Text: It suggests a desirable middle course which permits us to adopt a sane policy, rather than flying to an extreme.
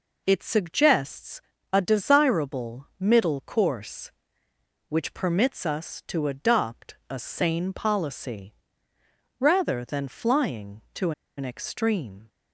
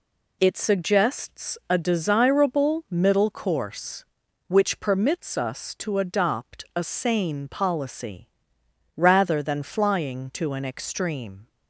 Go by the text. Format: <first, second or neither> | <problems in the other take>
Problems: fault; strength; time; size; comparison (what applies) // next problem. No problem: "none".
second | pauses between "suggests" and "a"; slight; at 1.4 s; 0.32 s long // pauses between "to" and "an"; slight; at 11.1 s; 0.26 s long